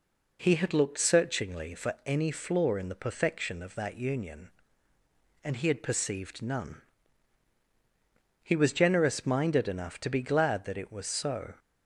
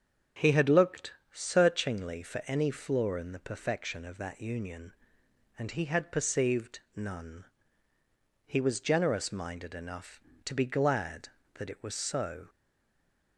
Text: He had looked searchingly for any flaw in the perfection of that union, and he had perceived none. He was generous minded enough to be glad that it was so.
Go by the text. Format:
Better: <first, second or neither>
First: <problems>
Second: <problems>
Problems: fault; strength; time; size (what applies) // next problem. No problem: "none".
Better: first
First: none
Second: starts louder than the rest; strong; until 1.5 s; 7.5 dB // pauses between "looked" and "searchingly"; slight; at 1.1 s; 0.18 s long // pauses between "perceived" and "none"; slight; at 6.7 s; 0.16 s long // stays silent after the last word; slight; from 12.4 s on; 0.9 s long